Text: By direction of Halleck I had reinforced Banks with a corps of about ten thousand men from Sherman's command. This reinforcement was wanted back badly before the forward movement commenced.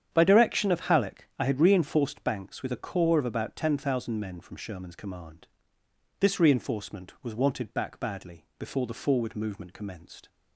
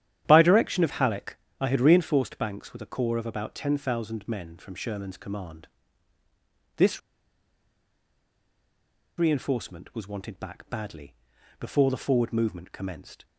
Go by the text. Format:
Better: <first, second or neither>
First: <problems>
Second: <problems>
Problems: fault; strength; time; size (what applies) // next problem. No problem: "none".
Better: first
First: starts louder than the rest; strong; until 1.1 s; 8.5 dB // pauses between "badly" and "before"; slight; at 8.4 s; 0.16 s long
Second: starts louder than the rest; strong; until 1.2 s; 11 dB // pauses between "Halleck" and "I"; slight; at 1.3 s; 0.24 s long // pauses between "This" and "reinforcement"; strong; at 7.0 s; 2.1 s long // pauses between "badly" and "before"; at 11.1 s; 0.44 s long